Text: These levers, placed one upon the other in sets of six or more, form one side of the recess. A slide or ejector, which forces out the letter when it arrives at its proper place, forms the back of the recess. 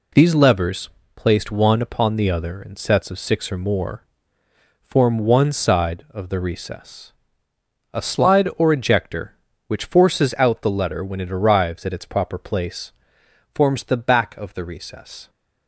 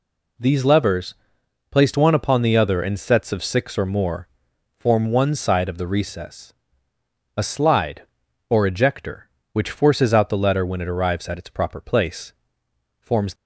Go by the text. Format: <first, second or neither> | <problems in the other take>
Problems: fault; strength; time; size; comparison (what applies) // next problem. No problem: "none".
first | stops before "the back of the recess"; at 13.3 s